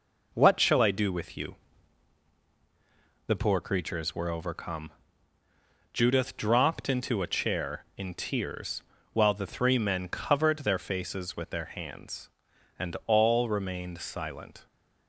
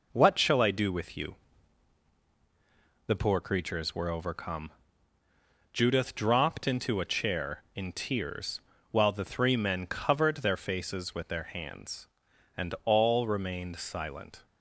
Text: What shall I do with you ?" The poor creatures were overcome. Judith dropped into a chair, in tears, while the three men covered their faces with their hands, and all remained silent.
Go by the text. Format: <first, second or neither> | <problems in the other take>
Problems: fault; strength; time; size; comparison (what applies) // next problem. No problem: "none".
neither | none